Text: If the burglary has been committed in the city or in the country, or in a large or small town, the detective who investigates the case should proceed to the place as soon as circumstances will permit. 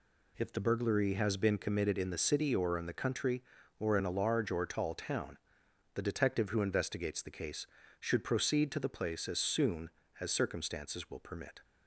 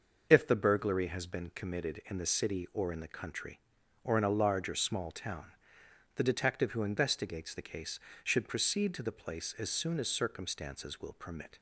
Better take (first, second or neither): second